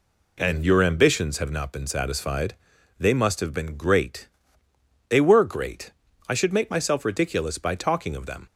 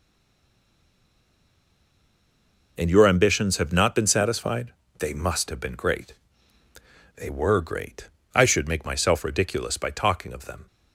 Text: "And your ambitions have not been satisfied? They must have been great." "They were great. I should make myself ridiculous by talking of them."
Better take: first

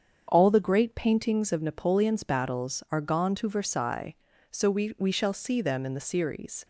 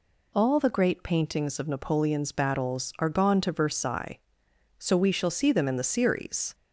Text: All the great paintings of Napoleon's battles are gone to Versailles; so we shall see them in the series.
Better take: second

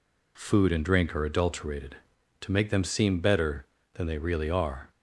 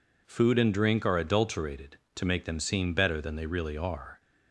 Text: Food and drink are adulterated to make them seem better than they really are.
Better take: neither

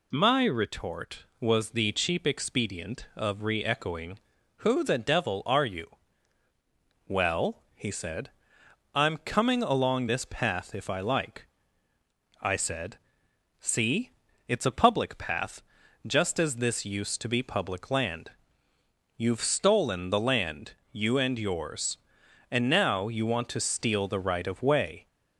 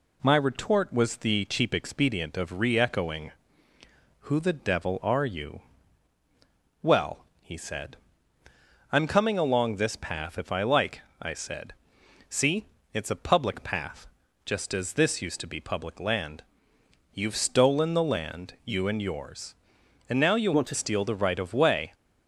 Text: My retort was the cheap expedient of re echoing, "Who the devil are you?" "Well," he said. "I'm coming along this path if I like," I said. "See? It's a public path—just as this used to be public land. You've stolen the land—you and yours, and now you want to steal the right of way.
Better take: first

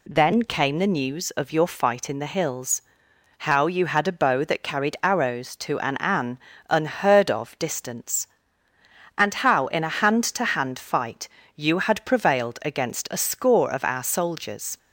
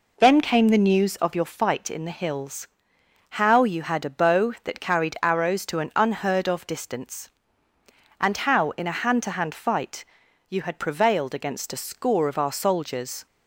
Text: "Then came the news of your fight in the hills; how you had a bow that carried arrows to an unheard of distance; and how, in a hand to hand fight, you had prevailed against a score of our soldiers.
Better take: second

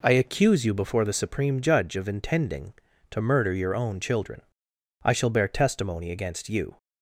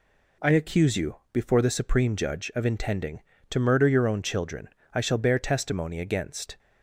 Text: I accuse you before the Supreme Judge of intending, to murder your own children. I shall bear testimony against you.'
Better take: first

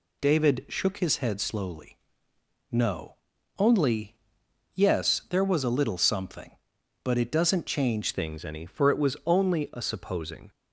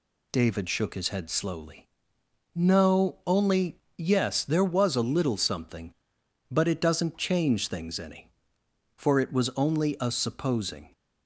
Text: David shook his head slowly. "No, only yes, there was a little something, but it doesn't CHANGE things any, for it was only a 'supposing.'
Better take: second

